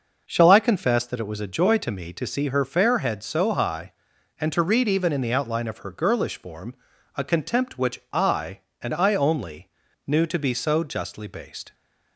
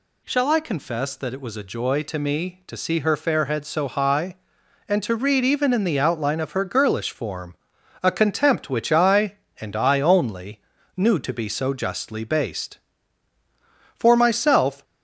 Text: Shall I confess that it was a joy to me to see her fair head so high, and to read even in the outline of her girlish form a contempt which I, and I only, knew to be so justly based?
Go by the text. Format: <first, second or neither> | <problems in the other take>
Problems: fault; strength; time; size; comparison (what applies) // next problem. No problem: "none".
first | pauses between "form" and "a"; noticeable; at 7.5 s; 0.47 s long; also in the first // goes on to say "For myself"; noticeable; from 13.9 s on; 0.88 s long